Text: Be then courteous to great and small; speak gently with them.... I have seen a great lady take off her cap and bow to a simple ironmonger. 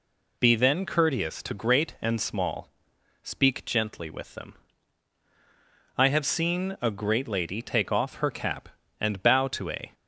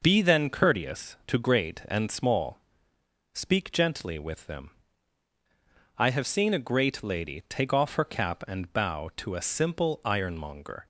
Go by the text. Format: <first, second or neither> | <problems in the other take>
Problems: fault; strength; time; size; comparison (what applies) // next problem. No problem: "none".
second | stops before "simple ironmonger"; at 9.9 s